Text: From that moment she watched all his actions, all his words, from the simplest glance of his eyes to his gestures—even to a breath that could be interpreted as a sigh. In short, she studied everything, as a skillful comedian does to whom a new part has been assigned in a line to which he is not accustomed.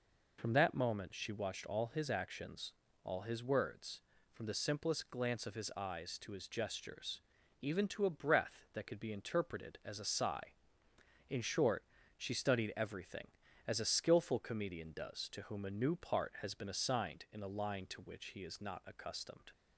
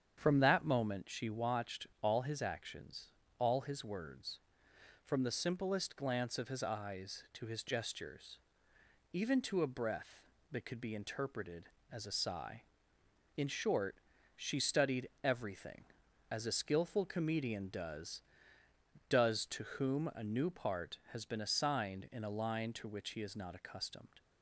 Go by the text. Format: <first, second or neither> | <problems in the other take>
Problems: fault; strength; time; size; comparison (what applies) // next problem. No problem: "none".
first | starts louder than the rest; strong; until 1.2 s; 8 dB // pauses between "studied" and "everything"; slight; at 15.0 s; 0.16 s long // says "does" twice; at 19.0 s